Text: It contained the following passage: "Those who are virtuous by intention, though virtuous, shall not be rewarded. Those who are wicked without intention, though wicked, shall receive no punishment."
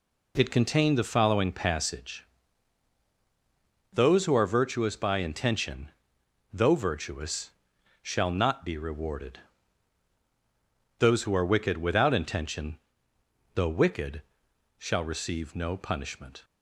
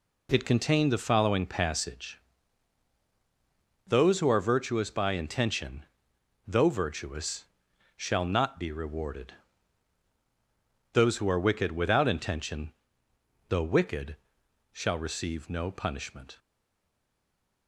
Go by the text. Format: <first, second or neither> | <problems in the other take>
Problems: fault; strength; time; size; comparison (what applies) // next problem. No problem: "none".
first | stays silent after the last word; noticeable; from 16.3 s on; 1.3 s long